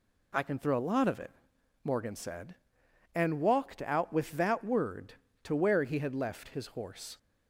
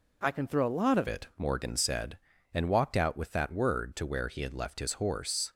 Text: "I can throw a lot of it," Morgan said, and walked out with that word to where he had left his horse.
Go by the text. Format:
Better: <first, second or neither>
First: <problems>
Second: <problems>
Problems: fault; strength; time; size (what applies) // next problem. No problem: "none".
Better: first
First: none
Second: changes voice at "it"; from 1.0 s on; 4.5 s long